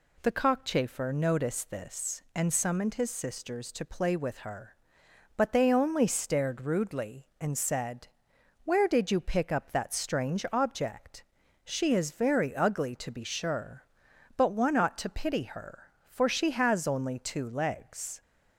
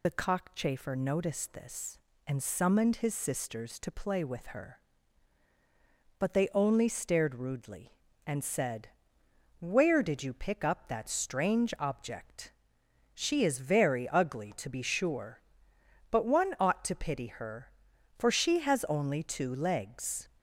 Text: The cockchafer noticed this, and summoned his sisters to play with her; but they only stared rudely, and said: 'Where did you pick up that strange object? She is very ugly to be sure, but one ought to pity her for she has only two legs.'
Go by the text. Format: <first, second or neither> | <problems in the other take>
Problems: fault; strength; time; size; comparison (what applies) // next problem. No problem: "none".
first | loses the start of "The"; at 0.0 s; 50 ms